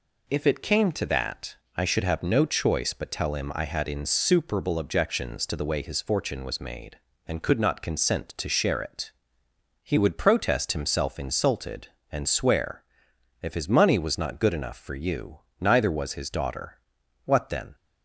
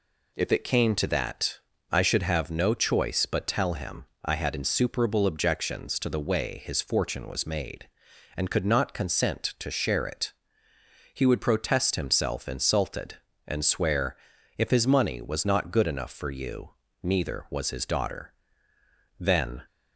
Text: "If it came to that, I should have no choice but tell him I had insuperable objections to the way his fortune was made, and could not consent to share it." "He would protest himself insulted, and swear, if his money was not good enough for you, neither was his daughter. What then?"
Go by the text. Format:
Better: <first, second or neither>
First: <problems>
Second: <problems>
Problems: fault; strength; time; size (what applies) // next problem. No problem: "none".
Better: first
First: none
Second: pauses between "him" and "I"; slight; at 4.0 s; 0.18 s long // skips "What"; at 18.7 s